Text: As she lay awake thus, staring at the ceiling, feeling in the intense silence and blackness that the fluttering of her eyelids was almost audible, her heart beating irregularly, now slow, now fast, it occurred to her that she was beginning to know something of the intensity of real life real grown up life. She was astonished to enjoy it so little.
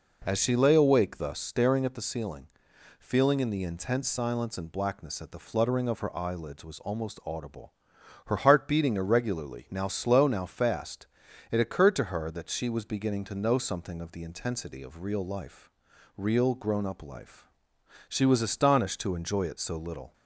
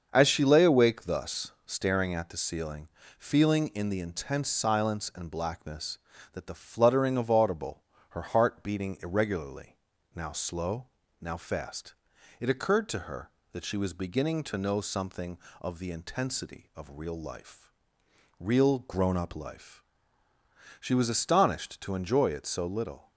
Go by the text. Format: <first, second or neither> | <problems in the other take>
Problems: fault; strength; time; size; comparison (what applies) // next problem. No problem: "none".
first | starts louder than the rest; until 1.1 s; 6.5 dB // skips "her eyelids was almost"; at 7.2 s // pauses between "life" and "real"; noticeable; at 17.6 s; 0.74 s long; also in the first